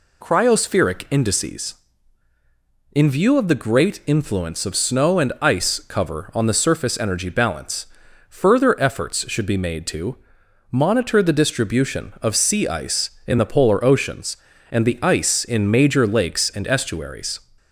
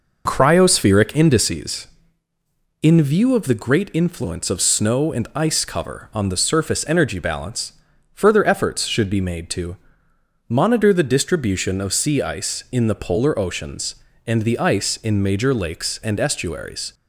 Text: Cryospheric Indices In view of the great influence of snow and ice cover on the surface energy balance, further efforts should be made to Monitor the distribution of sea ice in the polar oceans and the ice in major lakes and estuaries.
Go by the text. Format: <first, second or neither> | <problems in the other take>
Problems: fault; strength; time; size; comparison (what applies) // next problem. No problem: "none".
first | starts louder than the rest; noticeable; until 1.7 s; 5.5 dB // pauses between "to" and "Monitor"; noticeable; at 9.7 s; 0.72 s long; noticeable in the first